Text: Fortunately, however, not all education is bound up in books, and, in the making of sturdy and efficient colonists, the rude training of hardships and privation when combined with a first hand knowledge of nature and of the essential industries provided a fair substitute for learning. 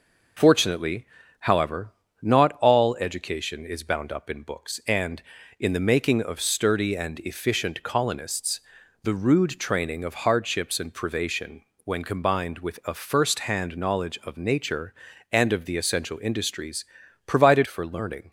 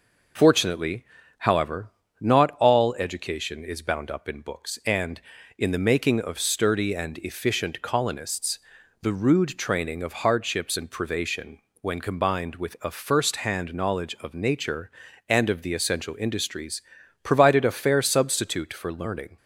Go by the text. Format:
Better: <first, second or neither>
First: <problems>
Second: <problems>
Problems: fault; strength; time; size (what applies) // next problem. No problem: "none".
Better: second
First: pauses between "privation" and "when"; slight; at 11.6 s; 0.22 s long // pauses between "industries" and "provided"; at 16.8 s; 0.40 s long // skips "a fair substitute"; at 17.6 s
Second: pauses between "privation" and "when"; slight; at 11.6 s; 0.22 s long // pauses between "industries" and "provided"; at 16.8 s; 0.40 s long